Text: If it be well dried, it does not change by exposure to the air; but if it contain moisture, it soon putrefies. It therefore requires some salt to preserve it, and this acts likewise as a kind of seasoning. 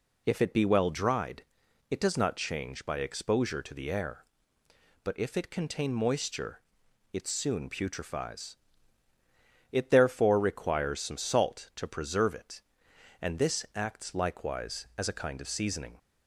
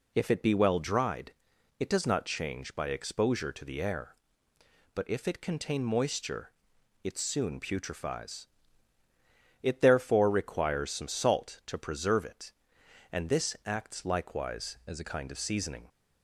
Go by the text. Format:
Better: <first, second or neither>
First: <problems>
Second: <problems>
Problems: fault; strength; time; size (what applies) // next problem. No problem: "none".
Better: first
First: none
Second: changes voice from "as" to "a"; from 14.8 to 15.0 s; 0.2 s long